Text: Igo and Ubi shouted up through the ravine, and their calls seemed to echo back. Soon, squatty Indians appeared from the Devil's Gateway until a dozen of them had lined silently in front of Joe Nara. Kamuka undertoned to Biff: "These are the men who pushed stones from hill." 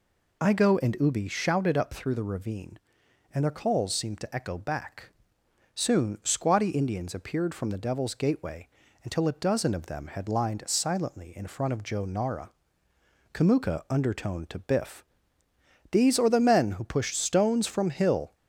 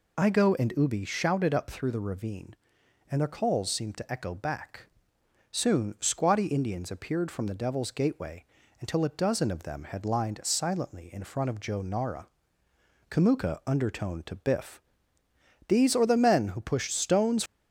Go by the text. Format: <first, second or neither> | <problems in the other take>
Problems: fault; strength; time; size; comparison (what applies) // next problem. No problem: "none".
first | pauses between "Gateway" and "until"; slight; at 8.4 s; 0.34 s long; slight in the first // stops before "from hill"; at 17.4 s